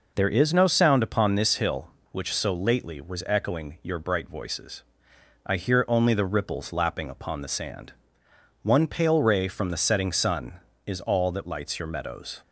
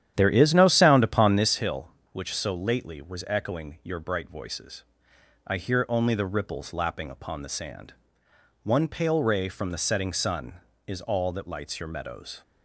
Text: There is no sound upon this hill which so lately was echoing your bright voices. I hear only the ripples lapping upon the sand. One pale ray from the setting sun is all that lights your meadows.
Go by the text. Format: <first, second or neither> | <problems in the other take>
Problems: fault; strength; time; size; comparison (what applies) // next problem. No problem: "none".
first | starts louder than the rest; strong; until 1.6 s; 10.5 dB